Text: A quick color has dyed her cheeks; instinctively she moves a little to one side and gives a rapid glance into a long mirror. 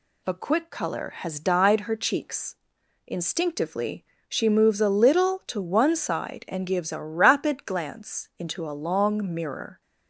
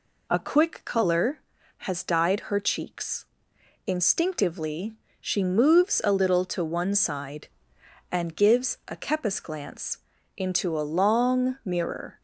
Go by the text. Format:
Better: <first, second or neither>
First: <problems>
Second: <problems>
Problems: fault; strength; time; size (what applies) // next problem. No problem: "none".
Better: first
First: pauses between "instinctively" and "she"; slight; at 4.0 s; 0.24 s long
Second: pauses between "instinctively" and "she"; slight; at 4.9 s; 0.24 s long // says "kepis" for "rapid"; at 8.9 s // pauses between "glance" and "into"; slight; at 9.9 s; 0.36 s long